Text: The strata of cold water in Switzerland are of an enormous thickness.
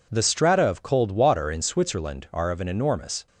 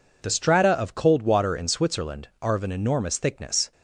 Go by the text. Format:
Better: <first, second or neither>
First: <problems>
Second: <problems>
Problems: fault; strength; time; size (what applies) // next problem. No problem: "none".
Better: second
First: stops before "thickness"; at 3.2 s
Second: none